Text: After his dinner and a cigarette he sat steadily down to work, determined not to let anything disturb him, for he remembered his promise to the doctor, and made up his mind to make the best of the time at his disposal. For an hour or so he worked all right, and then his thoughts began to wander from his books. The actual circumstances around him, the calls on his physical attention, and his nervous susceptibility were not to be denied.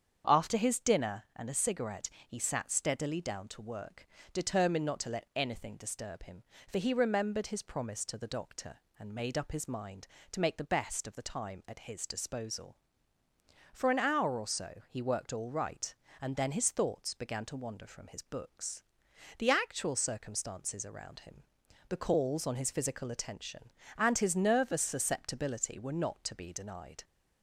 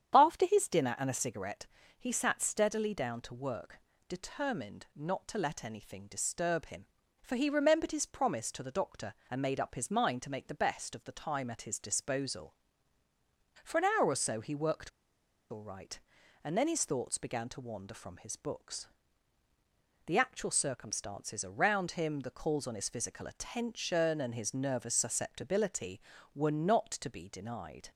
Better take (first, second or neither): first